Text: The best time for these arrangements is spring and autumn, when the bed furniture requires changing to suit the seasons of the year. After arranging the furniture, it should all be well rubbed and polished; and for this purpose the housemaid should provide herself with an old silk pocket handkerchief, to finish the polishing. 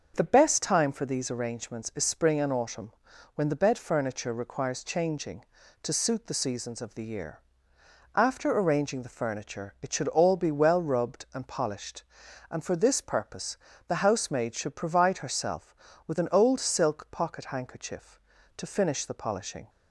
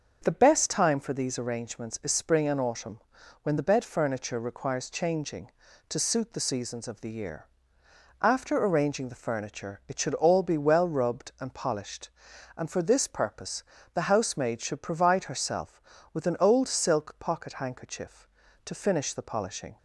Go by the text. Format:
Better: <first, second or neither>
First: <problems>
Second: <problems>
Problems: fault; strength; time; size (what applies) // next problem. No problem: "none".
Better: neither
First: starts louder than the rest; until 1.1 s; 6 dB // pauses between "purpose" and "the"; slight; at 13.5 s; 0.32 s long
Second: starts louder than the rest; until 1.2 s; 6 dB // pauses between "purpose" and "the"; slight; at 13.6 s; 0.32 s long